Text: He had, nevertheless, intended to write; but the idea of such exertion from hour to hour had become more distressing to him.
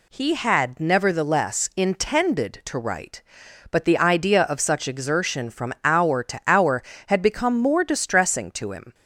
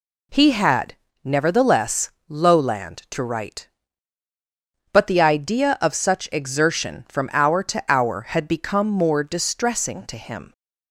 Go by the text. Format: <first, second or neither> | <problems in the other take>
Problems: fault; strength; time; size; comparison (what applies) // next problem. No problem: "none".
first | says "lowland" for "intended"; at 2.2 s